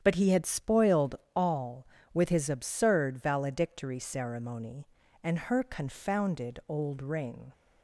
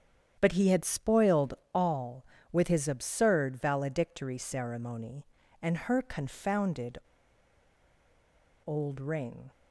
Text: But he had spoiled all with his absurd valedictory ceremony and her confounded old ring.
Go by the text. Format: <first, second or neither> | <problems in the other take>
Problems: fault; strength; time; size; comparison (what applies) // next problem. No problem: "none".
first | starts louder than the rest; strong; until 1.4 s; 9 dB; strong in the first // pauses between "spoiled" and "all"; slight; at 1.5 s; 0.22 s long; slight in the first // pauses between "confounded" and "old"; strong; at 6.9 s; 1.6 s long